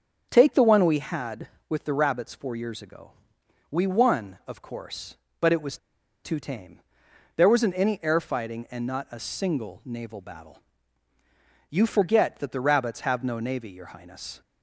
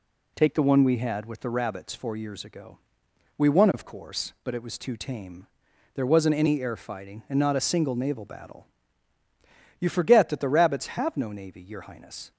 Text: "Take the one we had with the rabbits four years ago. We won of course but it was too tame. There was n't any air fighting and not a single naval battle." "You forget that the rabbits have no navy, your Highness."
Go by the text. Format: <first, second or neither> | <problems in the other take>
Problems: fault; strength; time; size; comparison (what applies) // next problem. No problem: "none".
second | starts louder than the rest; strong; until 1.3 s; 7.5 dB // pauses between "was" and "too"; noticeable; at 5.7 s; 0.47 s long